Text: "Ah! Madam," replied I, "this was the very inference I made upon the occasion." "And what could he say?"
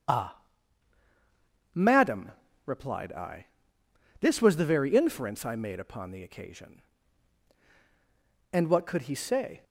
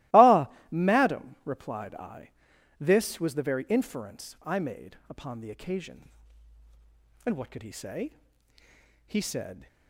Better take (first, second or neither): first